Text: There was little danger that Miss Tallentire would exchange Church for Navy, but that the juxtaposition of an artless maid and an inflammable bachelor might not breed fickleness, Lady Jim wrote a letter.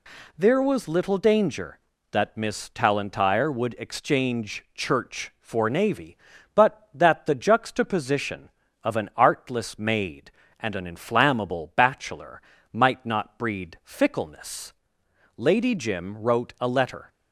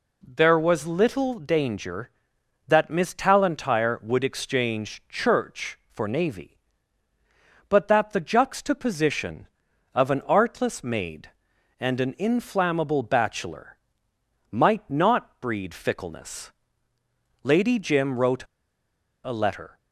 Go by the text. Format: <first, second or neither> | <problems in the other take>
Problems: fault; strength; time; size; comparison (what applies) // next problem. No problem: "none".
first | pauses between "bachelor" and "might"; noticeable; at 13.7 s; 0.74 s long; slight in the first // pauses between "wrote" and "a"; noticeable; at 18.4 s; 0.80 s long